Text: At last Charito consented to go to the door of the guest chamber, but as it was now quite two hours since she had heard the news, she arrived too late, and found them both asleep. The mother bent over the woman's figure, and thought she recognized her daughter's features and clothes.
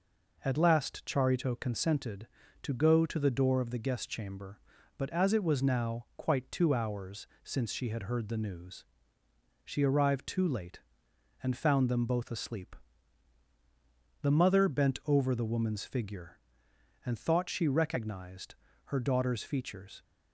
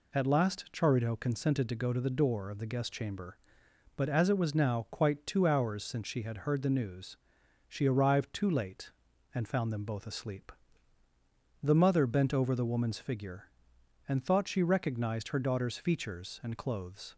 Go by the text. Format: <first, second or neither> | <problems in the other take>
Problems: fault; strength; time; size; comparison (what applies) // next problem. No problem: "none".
second | pauses between "hours" and "since"; slight; at 7.2 s; 0.16 s long // pauses between "recognized" and "her"; slight; at 18.5 s; 0.30 s long // stops before "and clothes"; at 20.0 s